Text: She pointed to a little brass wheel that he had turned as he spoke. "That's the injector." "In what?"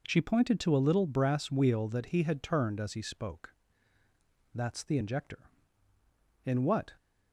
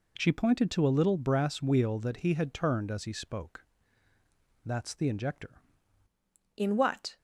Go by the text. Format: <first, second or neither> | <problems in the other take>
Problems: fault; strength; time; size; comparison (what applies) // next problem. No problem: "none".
first | changes voice at "In"; from 6.5 s on; 0.6 s long